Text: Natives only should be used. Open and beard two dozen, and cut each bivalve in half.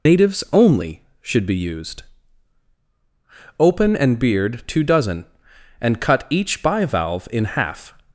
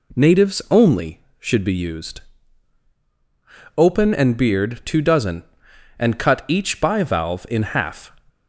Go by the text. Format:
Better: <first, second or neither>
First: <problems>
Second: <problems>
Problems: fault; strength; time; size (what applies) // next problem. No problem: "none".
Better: second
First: loses the start of "Natives"; at 0.0 s; 130 ms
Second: none